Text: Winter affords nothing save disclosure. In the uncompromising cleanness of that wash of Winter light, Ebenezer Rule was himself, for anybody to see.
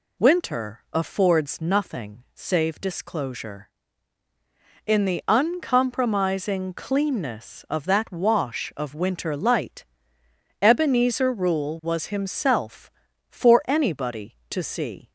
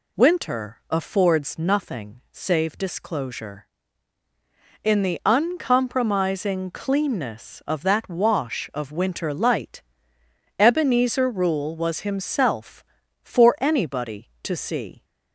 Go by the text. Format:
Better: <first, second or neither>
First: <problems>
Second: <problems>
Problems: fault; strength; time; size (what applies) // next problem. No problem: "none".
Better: neither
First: none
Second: none